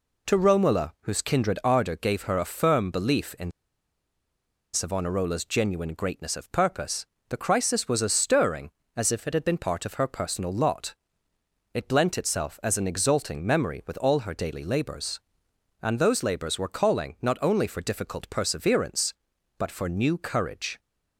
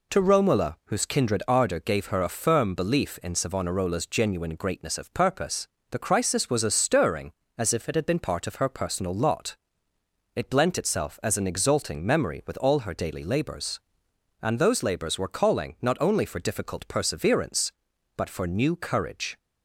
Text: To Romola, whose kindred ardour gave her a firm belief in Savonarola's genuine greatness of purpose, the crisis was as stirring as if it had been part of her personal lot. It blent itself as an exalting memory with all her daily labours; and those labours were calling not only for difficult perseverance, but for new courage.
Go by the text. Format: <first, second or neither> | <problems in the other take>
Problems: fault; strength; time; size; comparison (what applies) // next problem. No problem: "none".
second | pauses between "in" and "Savonarola's"; at 3.5 s; 1.2 s long